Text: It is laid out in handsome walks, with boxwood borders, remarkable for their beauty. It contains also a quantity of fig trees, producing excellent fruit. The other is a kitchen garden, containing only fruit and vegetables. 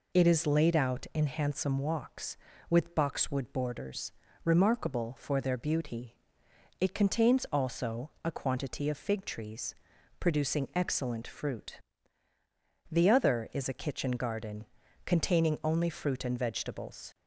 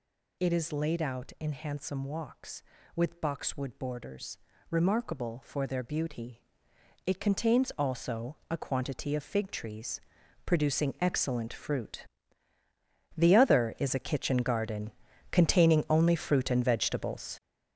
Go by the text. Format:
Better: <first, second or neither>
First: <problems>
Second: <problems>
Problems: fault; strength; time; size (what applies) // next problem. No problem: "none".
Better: first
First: none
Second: gets louder; strong; throughout; 9 dB